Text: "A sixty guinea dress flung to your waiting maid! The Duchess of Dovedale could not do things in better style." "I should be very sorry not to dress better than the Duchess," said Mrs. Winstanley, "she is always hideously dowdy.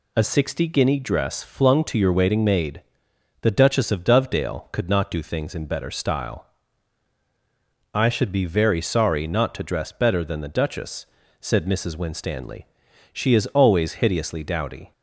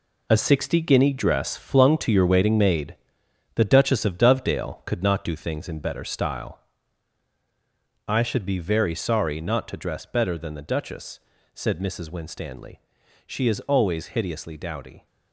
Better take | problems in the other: first | gets quieter; strong; throughout; 10 dB

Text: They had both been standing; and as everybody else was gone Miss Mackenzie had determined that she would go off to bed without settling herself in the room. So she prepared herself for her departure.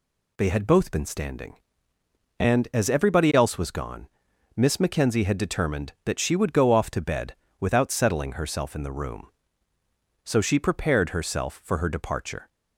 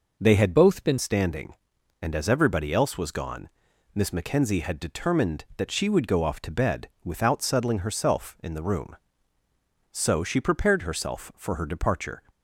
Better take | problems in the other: first | changes voice from "both" to "been"; from 0.5 to 0.9 s; 0.4 s long // pauses between "gone" and "Miss"; noticeable; at 3.4 s; 0.46 s long; noticeable in the first // pauses between "bed" and "without"; slight; at 6.8 s; 0.16 s long; slight in the first

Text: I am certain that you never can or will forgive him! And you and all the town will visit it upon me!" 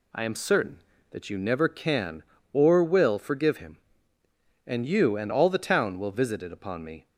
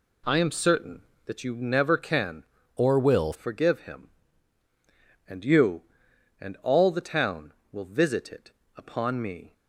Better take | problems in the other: first | changes voice from "or" to "will"; from 2.7 to 3.3 s; 0.6 s long // pauses between "it" and "upon"; slight; at 8.5 s; 0.24 s long

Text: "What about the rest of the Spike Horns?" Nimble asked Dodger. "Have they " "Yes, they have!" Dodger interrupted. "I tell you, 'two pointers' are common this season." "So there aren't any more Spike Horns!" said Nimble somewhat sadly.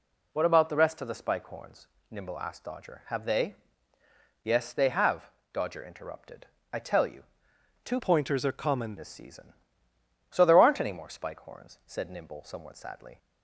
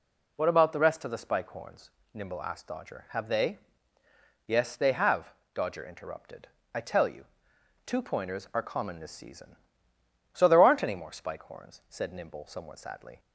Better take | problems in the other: second | changes voice from "pointers" to "common"; from 7.9 to 8.9 s; 1.0 s long

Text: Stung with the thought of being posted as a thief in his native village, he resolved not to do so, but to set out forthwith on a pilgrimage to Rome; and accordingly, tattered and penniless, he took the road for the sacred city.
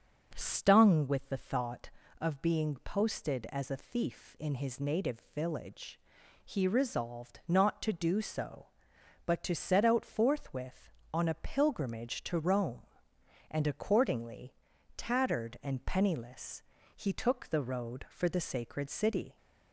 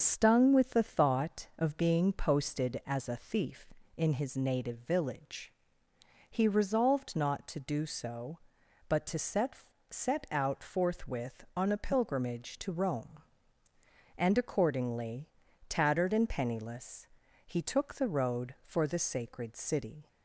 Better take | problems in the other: first | starts louder than the rest; noticeable; until 1.0 s; 6 dB // says "set" twice; at 9.9 s

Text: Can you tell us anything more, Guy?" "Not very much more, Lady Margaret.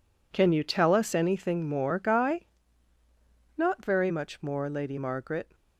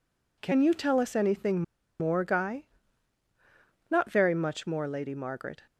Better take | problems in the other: first | pauses between "anything" and "more"; at 1.6 s; 0.38 s long

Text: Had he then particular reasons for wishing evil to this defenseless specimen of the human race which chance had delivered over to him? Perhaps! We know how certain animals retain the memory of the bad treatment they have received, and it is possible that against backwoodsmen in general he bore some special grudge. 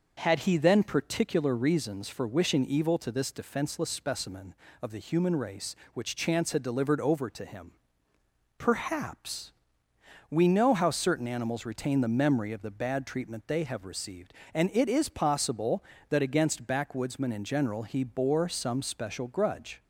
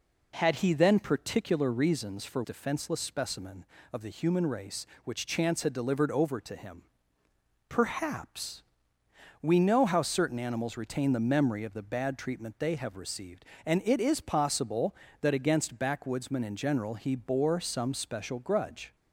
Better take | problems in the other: first | skips "wishing evil to this"; at 2.4 s

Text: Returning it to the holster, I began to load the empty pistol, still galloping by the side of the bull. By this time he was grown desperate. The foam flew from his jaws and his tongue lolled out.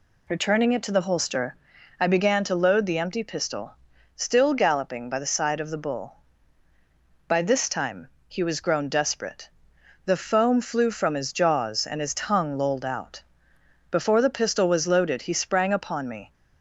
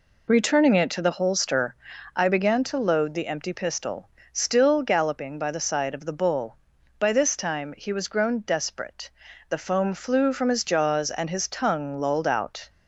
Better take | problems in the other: second | pauses between "time" and "he"; slight; at 8.0 s; 0.18 s long // goes on to say "Before the pistol was loaded he sprang upon me"; strong; from 13.8 s on; 2.4 s long

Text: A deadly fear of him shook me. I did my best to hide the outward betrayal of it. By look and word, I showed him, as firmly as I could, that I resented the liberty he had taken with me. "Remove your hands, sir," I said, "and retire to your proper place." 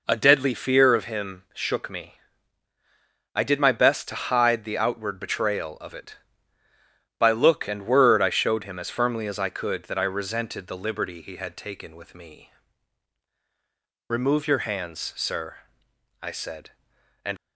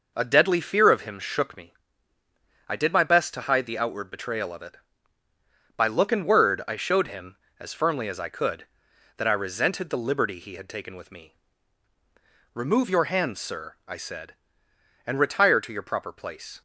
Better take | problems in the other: second | stops before "retire to your proper place"; at 17.3 s

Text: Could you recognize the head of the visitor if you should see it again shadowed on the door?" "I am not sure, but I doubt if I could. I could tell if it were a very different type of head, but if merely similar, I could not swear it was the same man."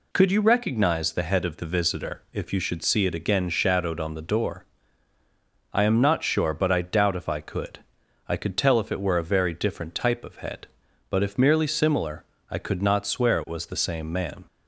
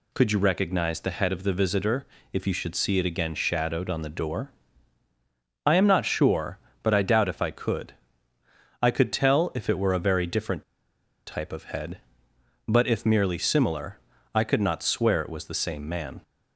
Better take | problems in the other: first | pauses between "visitor" and "if"; slight; at 2.0 s; 0.26 s long // pauses between "different" and "type"; noticeable; at 10.6 s; 0.63 s long

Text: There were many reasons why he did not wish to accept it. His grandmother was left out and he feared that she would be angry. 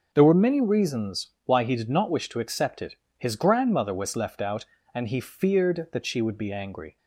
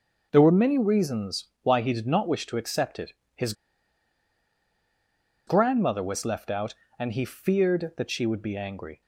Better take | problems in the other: first | starts louder than the rest; noticeable; until 1.3 s; 6 dB; noticeable in the first // pauses between "reasons" and "why"; slight; at 1.4 s; 0.16 s long; slight in the first // pauses between "His" and "grandmother"; strong; at 3.5 s; 1.9 s long

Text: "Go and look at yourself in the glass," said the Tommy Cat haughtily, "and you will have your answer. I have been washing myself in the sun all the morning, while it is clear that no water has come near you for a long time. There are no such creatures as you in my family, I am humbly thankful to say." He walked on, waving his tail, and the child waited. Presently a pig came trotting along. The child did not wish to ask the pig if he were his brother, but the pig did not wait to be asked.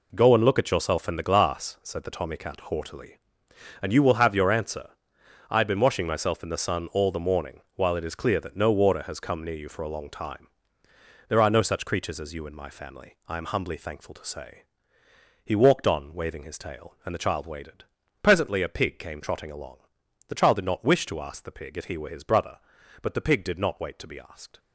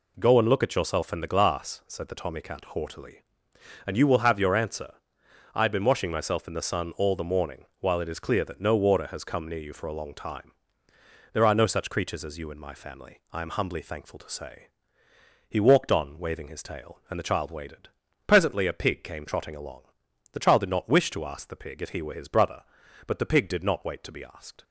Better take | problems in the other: second | gets quieter; strong; throughout; 10 dB

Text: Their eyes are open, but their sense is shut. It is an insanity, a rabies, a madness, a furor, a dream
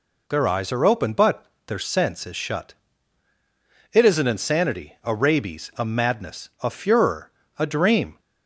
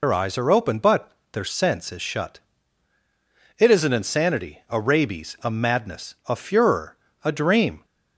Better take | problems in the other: first | loses the start of "Their"; at 0.0 s; 85 ms // pauses between "but" and "their"; slight; at 1.1 s; 0.22 s long; slight in the first

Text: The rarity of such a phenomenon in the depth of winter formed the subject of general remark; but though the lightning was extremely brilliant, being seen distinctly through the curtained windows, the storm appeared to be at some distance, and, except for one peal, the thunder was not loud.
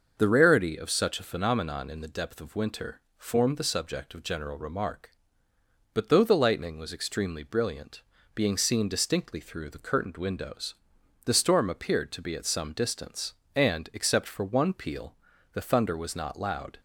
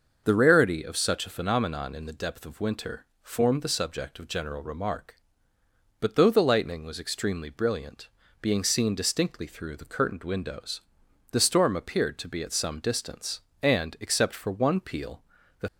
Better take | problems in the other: first | starts louder than the rest; noticeable; until 1.2 s; 6 dB; noticeable in the first // pauses between "winter" and "formed"; slight; at 3.0 s; 0.16 s long; slight in the first // stops before "thunder was not loud"; at 15.6 s

